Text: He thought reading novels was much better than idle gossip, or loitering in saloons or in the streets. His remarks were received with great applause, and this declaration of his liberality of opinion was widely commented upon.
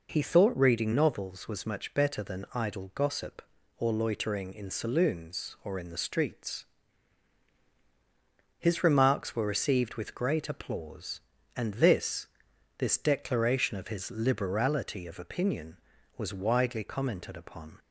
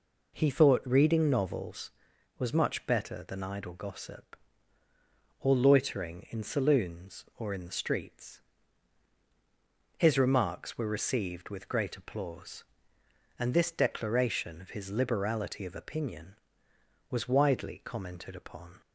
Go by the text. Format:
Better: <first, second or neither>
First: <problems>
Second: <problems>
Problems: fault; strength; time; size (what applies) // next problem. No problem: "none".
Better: second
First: says "this" twice; at 12.7 s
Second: none